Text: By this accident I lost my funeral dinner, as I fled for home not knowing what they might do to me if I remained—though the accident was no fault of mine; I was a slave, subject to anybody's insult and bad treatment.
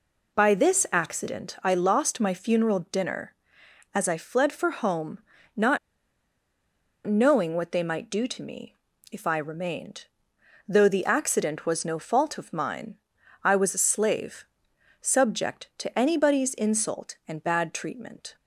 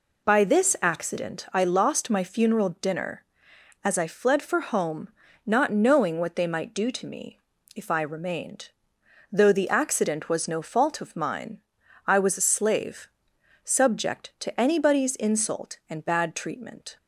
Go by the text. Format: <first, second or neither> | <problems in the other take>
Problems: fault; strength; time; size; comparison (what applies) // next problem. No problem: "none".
second | pauses between "home" and "not"; slight; at 5.1 s; 0.36 s long; slight in the second // pauses between "not" and "knowing"; strong; at 5.7 s; 1.2 s long // pauses between "me" and "if"; slight; at 8.7 s; 0.36 s long; slight in the second